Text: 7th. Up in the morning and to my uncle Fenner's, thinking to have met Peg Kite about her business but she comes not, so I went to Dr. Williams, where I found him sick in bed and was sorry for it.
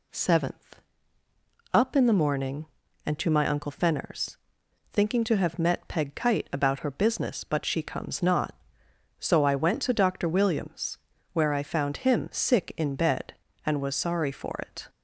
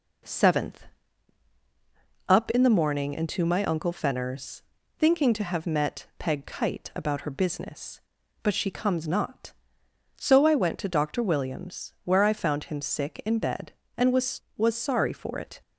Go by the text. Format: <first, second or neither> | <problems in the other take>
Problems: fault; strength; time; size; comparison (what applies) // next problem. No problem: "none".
first | says "was" twice; at 14.5 s